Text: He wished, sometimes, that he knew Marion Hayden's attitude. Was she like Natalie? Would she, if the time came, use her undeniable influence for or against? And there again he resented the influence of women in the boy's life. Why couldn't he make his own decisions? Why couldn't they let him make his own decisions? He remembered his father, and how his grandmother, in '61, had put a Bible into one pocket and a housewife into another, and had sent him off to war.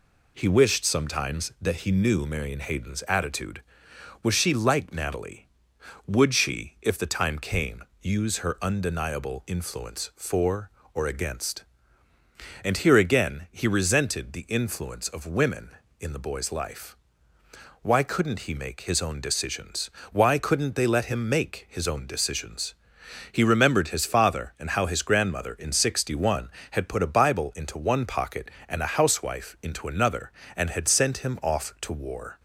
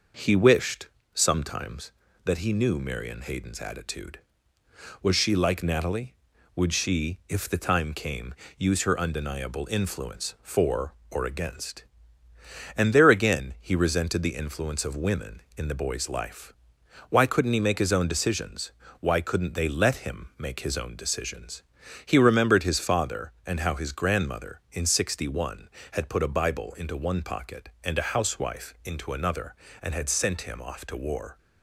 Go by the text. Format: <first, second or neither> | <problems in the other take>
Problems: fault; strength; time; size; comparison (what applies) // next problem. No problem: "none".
second | says "here" for "there"; at 12.7 s